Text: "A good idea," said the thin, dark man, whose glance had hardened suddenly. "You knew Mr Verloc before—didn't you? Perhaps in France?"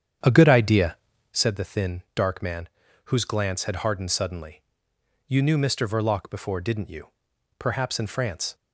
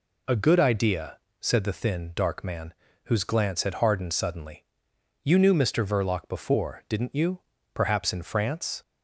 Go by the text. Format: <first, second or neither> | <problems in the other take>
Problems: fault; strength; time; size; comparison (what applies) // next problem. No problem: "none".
second | starts louder than the rest; strong; until 1.4 s; 8.5 dB